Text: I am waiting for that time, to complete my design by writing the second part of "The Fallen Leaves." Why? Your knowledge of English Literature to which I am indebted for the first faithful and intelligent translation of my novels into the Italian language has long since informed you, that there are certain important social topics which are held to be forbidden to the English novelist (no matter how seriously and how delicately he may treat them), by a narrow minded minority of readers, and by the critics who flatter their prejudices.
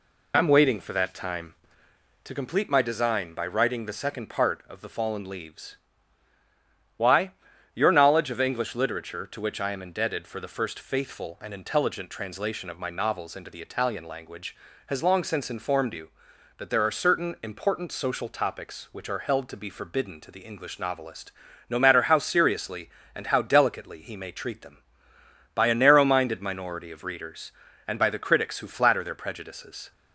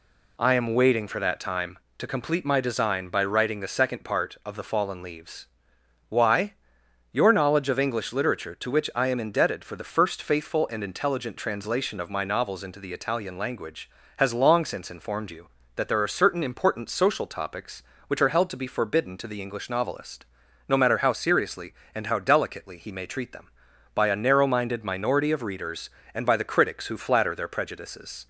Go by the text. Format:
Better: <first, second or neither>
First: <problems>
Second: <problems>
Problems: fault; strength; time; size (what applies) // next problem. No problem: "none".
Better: neither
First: none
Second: none